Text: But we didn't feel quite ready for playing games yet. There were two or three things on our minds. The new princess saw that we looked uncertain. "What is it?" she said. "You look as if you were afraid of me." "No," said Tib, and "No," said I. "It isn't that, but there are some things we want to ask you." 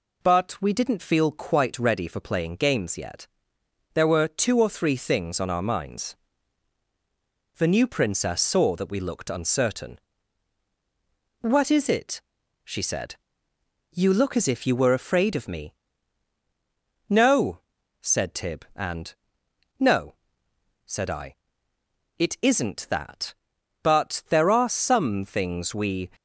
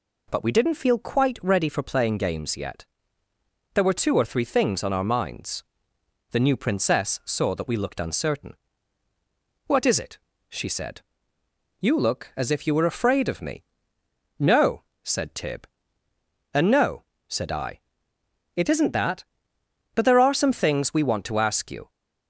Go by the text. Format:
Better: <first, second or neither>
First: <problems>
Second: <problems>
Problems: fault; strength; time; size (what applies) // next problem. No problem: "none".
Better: second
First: pauses between "and" and "No"; noticeable; at 19.1 s; 0.66 s long // stops before "want to ask you"; at 26.1 s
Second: none